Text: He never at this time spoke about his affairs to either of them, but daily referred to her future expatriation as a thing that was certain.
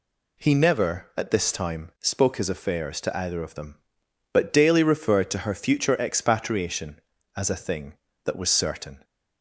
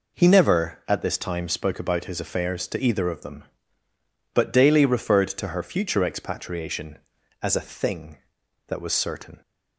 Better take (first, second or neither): second